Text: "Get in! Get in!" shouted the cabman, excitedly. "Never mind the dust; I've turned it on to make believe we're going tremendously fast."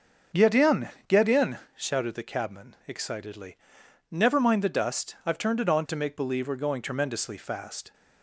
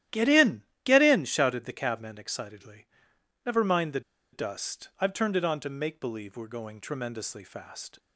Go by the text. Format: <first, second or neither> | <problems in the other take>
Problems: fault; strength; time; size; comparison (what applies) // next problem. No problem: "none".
first | starts louder than the rest; strong; until 1.3 s; 12.5 dB; also in the first // pauses between "the" and "dust"; slight; at 4.0 s; 0.32 s long